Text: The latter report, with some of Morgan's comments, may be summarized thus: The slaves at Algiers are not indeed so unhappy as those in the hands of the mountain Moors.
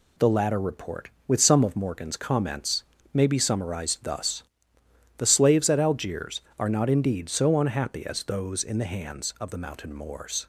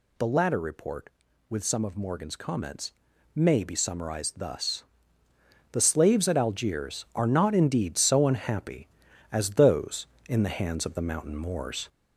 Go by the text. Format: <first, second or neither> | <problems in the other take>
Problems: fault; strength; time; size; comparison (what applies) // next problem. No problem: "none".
first | gets louder; slight; throughout; 2.5 dB